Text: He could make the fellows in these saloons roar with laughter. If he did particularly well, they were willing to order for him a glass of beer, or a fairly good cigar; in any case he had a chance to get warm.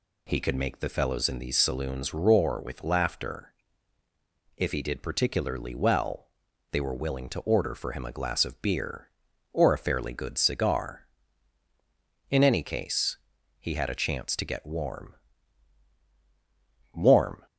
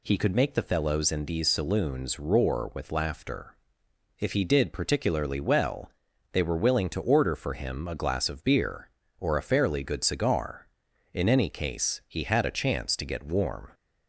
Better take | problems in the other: second | pauses between "case" and "he"; at 13.1 s; 0.42 s long // says "warm" twice; at 16.9 s

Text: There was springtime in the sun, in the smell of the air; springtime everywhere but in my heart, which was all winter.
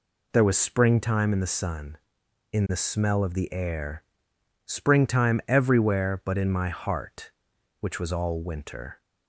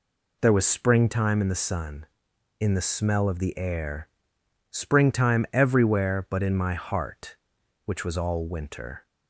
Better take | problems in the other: neither | none

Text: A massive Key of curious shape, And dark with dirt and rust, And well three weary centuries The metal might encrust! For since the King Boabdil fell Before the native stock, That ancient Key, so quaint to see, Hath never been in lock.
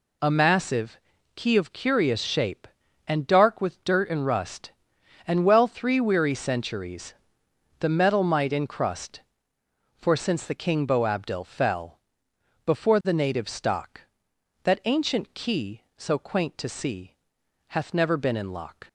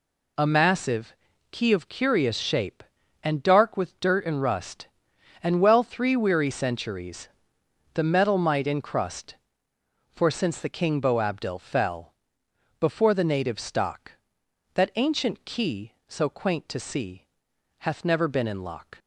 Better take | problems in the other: neither | pauses between "massive" and "Key"; the same in both // pauses between "centuries" and "The"; noticeable; the same in both // pauses between "fell" and "Before"; noticeable; the same in both

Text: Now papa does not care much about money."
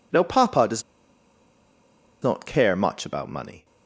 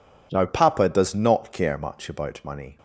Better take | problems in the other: second | pauses between "does" and "not"; strong; at 0.8 s; 1.4 s long

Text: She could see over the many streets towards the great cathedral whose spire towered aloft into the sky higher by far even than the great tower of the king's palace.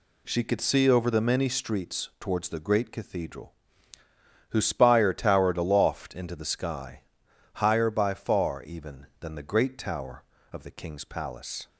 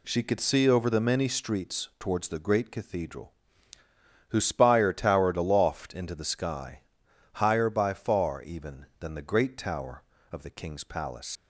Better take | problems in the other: first | pauses between "cathedral" and "whose"; noticeable; at 3.3 s; 0.96 s long; noticeable in the first // pauses between "sky" and "higher"; noticeable; at 6.8 s; 0.52 s long; noticeable in the first // leaves "palace" unfinished; at 11.3 s; 120 ms

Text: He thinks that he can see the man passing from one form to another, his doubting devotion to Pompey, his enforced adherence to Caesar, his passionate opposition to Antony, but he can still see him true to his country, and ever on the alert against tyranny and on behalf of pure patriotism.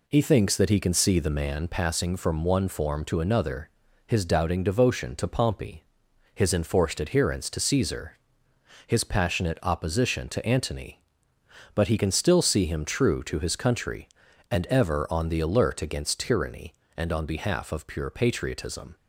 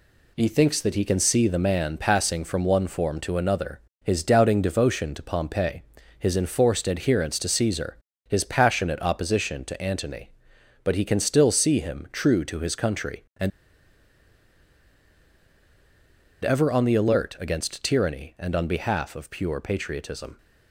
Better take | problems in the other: first | pauses between "and" and "ever"; strong; at 13.5 s; 2.9 s long

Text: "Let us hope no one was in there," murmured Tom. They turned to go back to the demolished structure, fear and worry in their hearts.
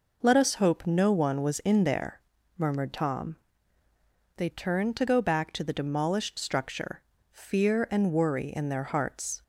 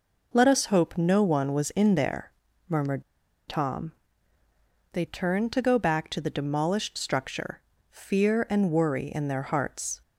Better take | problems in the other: first | pauses between "murmured" and "Tom"; noticeable; at 3.0 s; 0.46 s long

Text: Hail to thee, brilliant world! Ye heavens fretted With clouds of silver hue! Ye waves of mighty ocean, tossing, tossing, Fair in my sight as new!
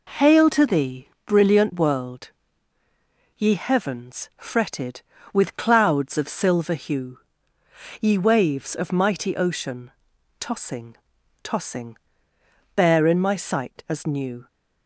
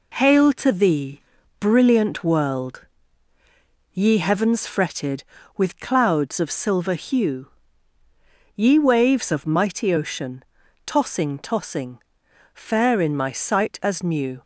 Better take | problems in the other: second | says "Bare" for "Fair"; at 12.7 s

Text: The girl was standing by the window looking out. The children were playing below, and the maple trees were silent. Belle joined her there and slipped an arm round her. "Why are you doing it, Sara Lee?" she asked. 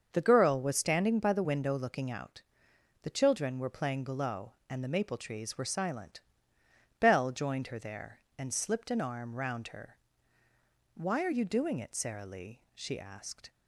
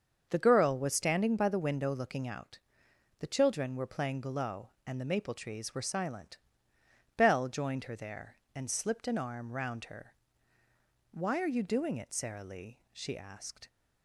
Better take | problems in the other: neither | starts louder than the rest; the same in both

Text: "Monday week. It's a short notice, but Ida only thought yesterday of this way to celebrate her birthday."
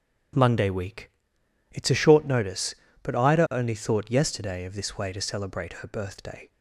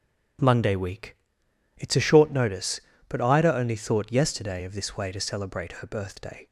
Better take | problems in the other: neither | starts louder than the rest; strong; the same in both

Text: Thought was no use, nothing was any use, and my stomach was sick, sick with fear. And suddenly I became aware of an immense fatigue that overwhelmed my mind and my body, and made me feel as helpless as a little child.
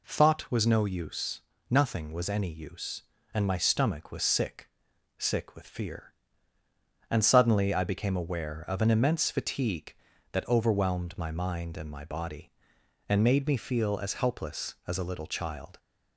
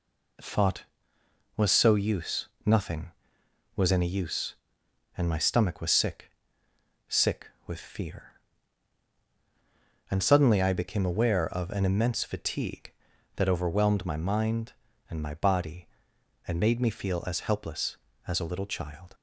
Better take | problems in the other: first | says "so" for "no"; at 1.7 s

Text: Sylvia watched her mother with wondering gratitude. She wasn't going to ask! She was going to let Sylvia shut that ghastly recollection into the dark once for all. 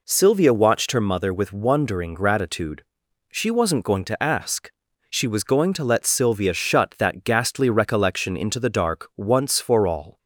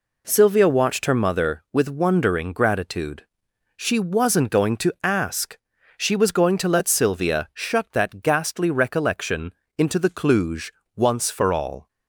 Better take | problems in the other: first | pauses between "recollection" and "into"; slight; at 9.5 s; 0.26 s long // says "cluj" for "dark"; at 10.0 s

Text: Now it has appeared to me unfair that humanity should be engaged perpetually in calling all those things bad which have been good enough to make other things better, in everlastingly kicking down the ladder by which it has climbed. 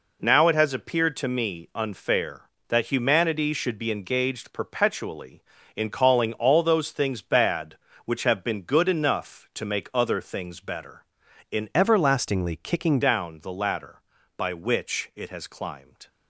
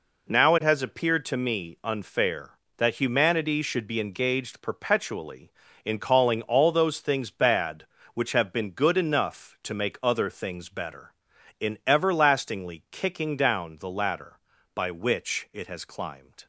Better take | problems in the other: second | changes voice from "everlastingly" to "kicking"; from 11.7 to 13.0 s; 1.3 s long

